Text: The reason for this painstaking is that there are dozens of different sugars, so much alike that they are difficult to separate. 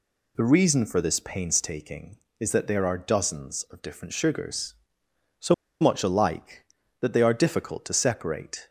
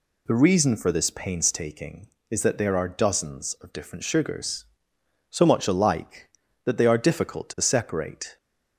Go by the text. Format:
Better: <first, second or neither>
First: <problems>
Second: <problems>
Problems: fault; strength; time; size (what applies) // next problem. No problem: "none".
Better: second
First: pauses between "so" and "much"; slight; at 5.5 s; 0.26 s long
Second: none